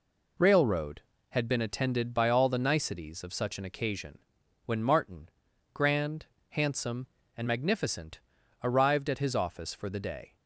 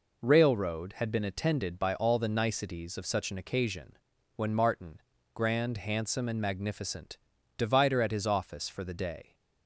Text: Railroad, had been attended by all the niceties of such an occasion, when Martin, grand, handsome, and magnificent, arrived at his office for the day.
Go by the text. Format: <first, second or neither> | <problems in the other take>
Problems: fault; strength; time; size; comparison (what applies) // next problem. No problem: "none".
first | says "divider" for "arrived"; at 7.5 s